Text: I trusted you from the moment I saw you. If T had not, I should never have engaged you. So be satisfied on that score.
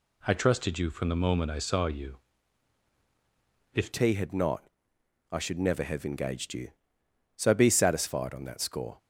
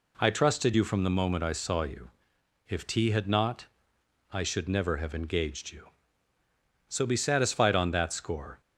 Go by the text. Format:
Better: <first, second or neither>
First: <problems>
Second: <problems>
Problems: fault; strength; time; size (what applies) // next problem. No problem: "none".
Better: second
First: changes voice at "T"; from 3.9 s on; 5.0 s long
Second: none